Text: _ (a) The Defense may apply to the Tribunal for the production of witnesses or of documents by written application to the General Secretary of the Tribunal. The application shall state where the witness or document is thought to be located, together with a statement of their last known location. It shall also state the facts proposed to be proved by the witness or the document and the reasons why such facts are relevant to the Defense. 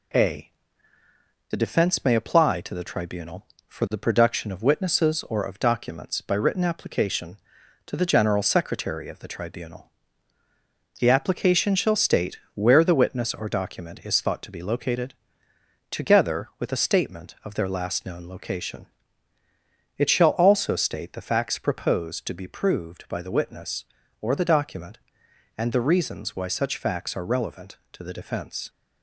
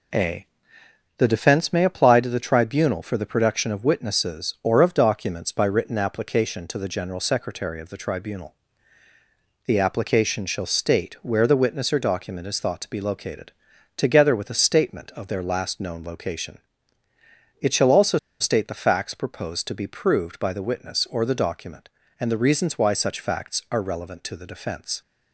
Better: first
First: none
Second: pauses between "also" and "state"; slight; at 18.1 s; 0.22 s long

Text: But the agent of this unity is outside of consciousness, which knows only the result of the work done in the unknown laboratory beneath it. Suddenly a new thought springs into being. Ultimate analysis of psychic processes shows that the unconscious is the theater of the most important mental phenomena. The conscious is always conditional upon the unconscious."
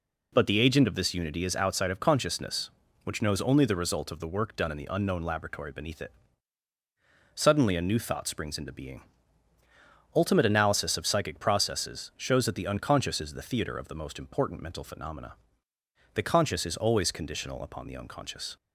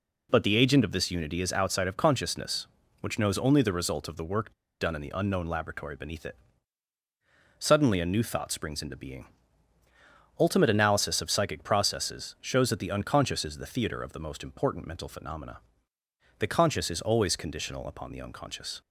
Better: first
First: none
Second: pauses between "work" and "done"; slight; at 4.5 s; 0.27 s long

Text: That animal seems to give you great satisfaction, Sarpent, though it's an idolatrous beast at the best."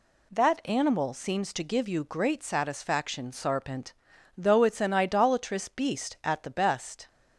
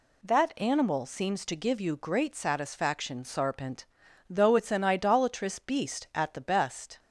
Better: neither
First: none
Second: none

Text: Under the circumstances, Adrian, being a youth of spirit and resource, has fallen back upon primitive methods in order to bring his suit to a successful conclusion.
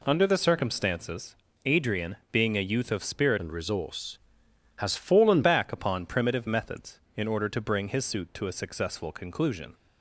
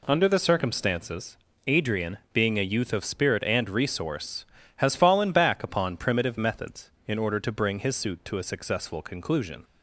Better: second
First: changes voice from "and" to "fallen"; from 3.3 to 5.4 s; 2.1 s long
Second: none

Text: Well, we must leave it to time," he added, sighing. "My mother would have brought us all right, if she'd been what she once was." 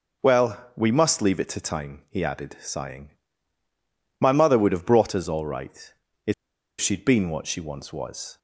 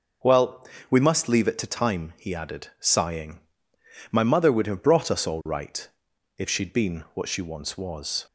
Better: second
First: pauses between "if" and "she'd"; noticeable; at 6.3 s; 0.45 s long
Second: none

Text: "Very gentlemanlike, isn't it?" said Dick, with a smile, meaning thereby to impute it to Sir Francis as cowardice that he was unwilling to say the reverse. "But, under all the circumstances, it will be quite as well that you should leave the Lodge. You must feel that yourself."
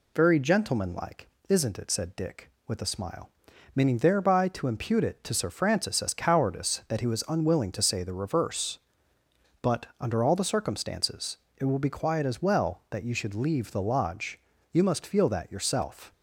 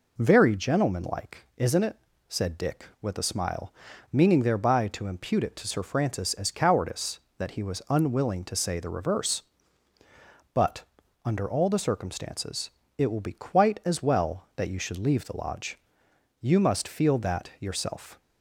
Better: second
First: says "quiet" for "quite"; at 11.8 s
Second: none

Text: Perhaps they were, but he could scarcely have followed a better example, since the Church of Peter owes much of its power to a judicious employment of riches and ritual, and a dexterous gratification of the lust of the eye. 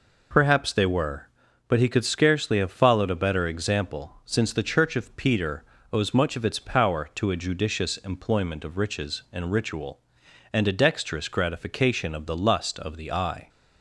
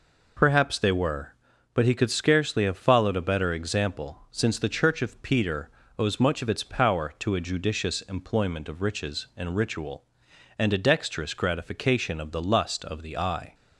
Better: neither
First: pauses between "Peter" and "owes"; slight; at 5.6 s; 0.30 s long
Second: pauses between "Peter" and "owes"; slight; at 5.6 s; 0.30 s long

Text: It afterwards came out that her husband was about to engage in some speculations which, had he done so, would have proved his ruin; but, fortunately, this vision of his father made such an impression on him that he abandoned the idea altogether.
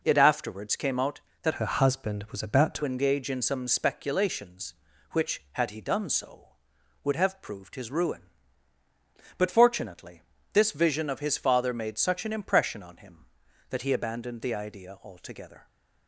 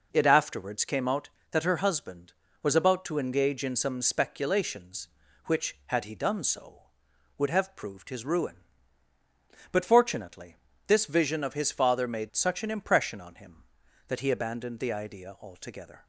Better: second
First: changes voice from "her" to "to"; from 1.5 to 2.8 s; 1.3 s long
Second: none

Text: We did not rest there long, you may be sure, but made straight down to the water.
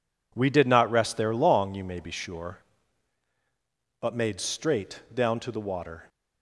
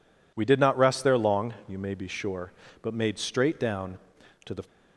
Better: first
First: none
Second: stops before "water"; at 4.6 s

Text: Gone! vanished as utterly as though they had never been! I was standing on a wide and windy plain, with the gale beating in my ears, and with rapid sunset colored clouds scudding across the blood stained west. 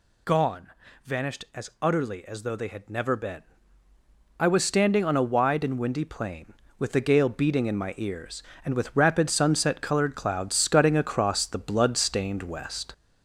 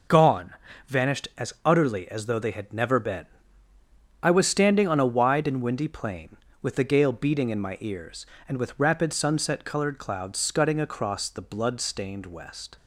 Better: second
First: gets louder; throughout; 4 dB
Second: none

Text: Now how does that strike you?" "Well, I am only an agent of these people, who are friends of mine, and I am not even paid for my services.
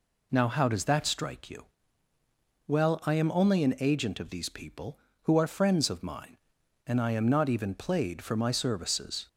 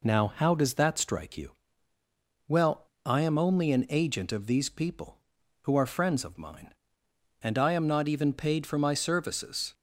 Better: second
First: says "played" for "paid"; at 7.7 s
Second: none

